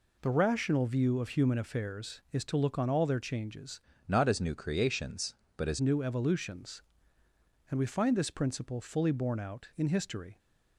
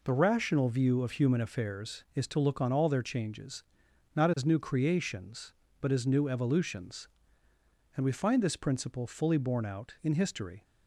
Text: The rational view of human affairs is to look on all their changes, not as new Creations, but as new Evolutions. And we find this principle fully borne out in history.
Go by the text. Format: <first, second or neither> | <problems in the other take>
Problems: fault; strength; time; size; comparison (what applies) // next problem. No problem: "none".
second | changes voice from "not" to "as"; from 4.0 to 5.7 s; 1.7 s long